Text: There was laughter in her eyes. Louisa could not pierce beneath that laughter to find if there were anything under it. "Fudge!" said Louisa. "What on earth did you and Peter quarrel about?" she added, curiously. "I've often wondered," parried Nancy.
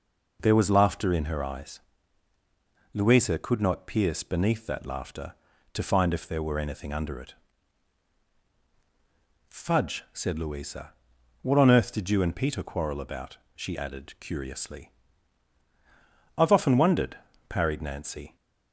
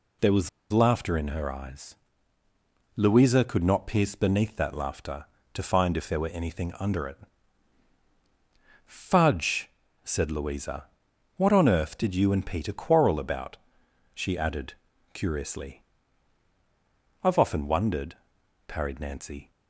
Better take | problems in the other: first | pauses between "was" and "laughter"; slight; at 0.4 s; 0.22 s long

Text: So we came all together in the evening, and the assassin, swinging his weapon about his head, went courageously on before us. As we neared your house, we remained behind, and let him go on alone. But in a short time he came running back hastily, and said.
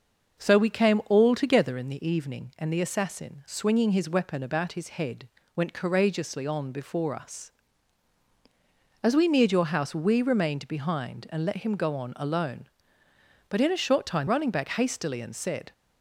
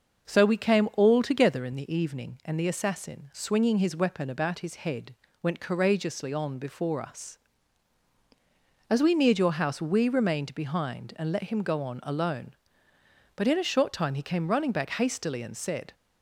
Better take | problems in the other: second | starts louder than the rest; noticeable; until 1.4 s; 6 dB; noticeable in the second // skips "he came"; at 14.2 s

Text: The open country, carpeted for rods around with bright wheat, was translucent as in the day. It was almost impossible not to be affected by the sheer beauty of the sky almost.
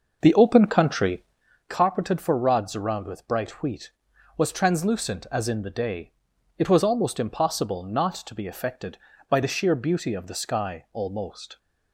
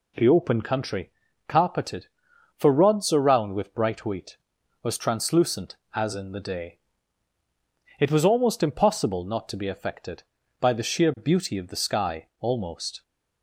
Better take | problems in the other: second | starts louder than the rest; noticeable; until 1.5 s; 6 dB

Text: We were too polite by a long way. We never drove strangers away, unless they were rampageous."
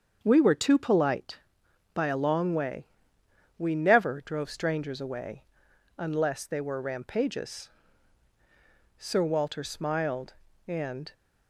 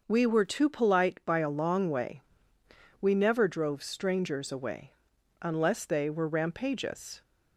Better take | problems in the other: second | starts louder than the rest; until 1.2 s; 7 dB; noticeable in the second // goes on to say "Sir Walter smiled and"; strong; from 8.9 s on; 2.1 s long

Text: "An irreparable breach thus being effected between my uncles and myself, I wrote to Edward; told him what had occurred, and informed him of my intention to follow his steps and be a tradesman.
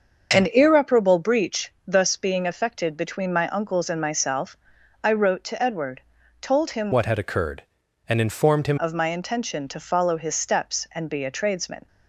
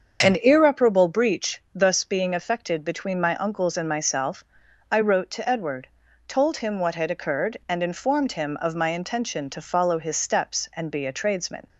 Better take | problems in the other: second | starts louder than the rest; until 1.4 s; 6.5 dB; also in the second // changes voice from "what" to "him"; from 6.9 to 8.7 s; 1.8 s long

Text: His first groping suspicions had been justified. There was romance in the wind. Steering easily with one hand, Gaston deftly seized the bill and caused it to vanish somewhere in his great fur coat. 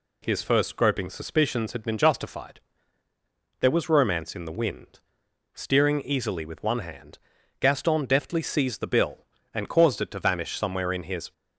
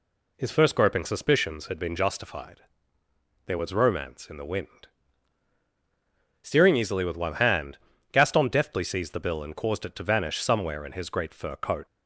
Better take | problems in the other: second | stops before "great fur coat"; at 11.3 s

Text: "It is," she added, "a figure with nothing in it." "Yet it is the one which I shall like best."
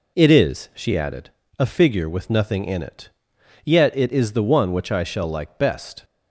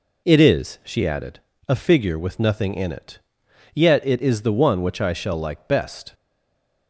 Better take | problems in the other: first | stays silent after the last word; slight; from 6.1 s on; 0.7 s long

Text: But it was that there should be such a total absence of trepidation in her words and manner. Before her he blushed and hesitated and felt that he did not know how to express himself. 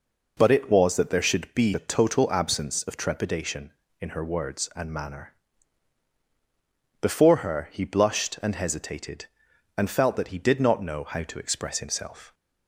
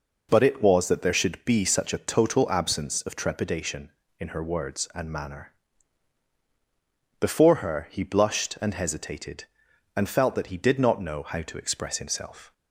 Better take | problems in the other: second | skips "such"; at 1.7 s

